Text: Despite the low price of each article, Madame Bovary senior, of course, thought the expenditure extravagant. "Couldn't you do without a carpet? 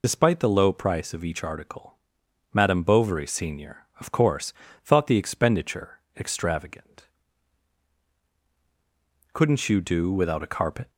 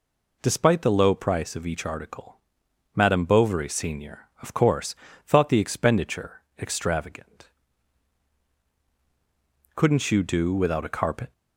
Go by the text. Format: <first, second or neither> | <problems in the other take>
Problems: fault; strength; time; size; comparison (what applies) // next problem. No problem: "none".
second | loses the start of "Despite"; at 0.0 s; 60 ms // pauses between "expenditure" and "extravagant"; slight; at 5.9 s; 0.18 s long; slight in the second